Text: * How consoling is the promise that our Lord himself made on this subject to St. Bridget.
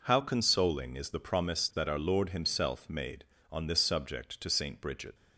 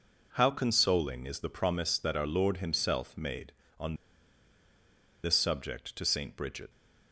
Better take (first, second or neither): first